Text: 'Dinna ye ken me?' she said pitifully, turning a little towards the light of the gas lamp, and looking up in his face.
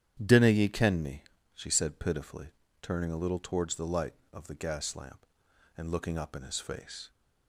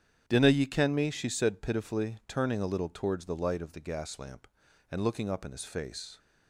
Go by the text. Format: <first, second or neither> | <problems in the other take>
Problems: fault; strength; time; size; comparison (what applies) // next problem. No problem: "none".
neither | starts louder than the rest; strong; the same in both